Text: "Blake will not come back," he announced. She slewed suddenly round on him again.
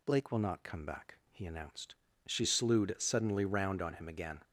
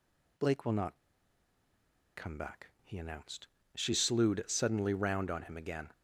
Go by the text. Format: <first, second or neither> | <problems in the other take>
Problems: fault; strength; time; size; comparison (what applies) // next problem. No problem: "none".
first | pauses between "not" and "come"; at 0.9 s; 1.1 s long